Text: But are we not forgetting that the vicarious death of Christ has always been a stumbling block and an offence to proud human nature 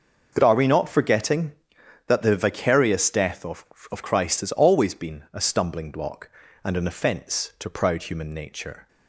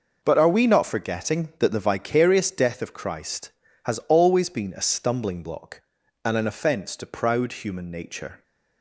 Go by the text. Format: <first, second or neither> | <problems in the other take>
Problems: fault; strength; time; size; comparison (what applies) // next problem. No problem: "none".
second | starts louder than the rest; until 1.3 s; 6.5 dB // says "of" twice; at 3.9 s